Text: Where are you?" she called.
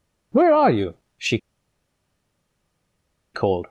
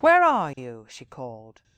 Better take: second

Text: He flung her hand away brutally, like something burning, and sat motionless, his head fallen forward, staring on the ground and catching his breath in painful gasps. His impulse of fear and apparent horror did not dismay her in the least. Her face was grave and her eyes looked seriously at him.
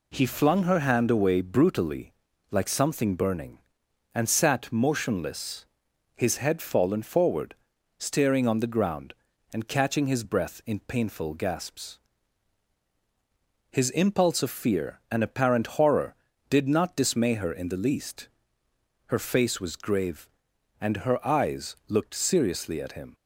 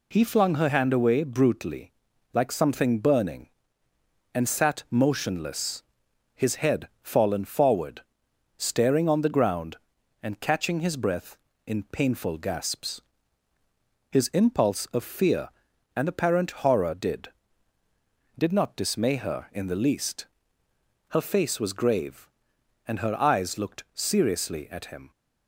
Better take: first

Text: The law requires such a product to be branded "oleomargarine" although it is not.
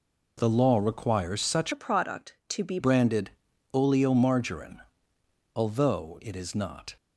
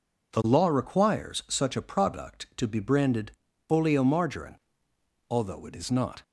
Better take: second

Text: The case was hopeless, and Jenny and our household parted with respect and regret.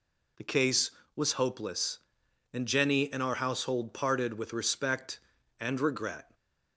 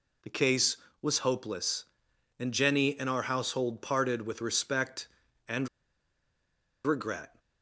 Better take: first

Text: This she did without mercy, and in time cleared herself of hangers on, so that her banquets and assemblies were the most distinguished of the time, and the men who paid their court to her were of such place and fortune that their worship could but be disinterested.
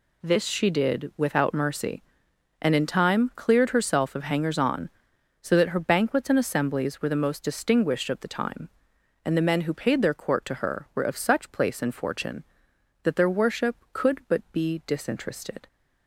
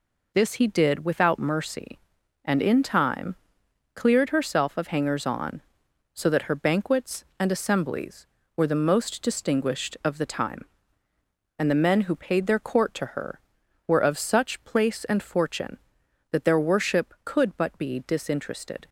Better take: first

